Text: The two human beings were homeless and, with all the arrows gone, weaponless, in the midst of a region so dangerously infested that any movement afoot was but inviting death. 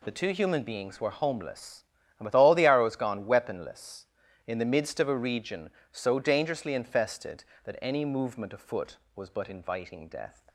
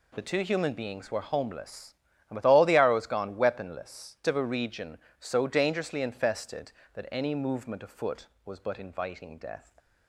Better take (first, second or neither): first